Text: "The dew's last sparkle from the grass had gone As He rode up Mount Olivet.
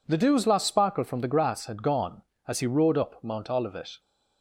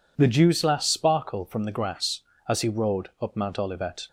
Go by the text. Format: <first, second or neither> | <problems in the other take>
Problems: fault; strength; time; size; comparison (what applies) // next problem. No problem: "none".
first | skips "had gone"; at 2.3 s